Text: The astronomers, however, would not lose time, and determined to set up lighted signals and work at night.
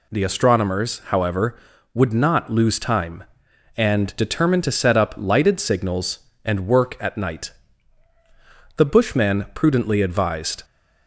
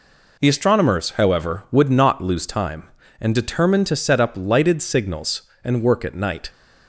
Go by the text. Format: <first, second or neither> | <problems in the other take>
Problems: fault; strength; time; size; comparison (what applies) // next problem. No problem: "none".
second | goes on to say "The bushman prudently advised"; strong; from 8.7 s on; 1.8 s long